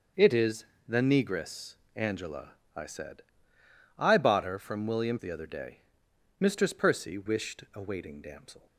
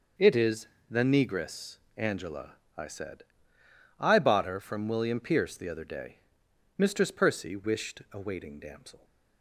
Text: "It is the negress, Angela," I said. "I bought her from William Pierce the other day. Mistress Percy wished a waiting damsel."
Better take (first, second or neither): second